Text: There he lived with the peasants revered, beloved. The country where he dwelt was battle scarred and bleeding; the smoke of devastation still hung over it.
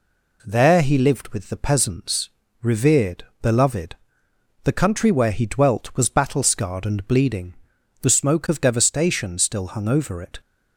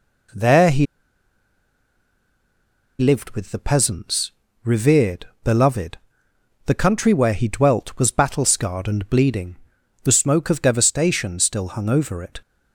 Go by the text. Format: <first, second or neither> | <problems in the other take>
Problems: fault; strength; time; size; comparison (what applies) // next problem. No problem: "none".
first | pauses between "he" and "lived"; strong; at 0.8 s; 2.1 s long // pauses between "peasants" and "revered"; slight; at 4.3 s; 0.34 s long; slight in the first